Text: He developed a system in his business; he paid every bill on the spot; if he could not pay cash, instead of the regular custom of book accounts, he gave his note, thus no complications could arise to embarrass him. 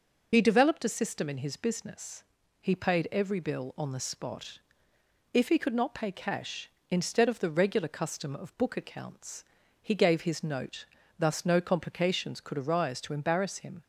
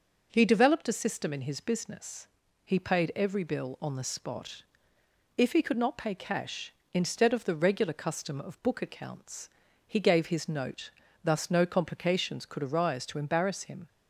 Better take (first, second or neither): second